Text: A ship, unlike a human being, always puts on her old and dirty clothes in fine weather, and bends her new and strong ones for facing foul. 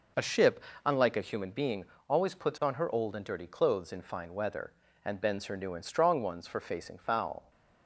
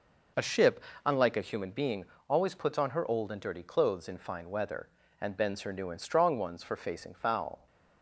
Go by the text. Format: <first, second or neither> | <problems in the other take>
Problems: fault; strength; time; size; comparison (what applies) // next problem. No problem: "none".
neither | none